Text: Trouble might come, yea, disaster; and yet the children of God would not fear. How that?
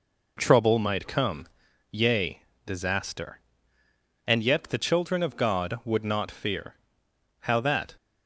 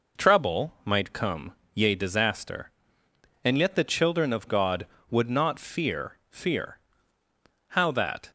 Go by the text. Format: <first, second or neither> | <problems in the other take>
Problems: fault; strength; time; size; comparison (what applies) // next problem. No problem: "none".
first | says "fear" twice; at 6.3 s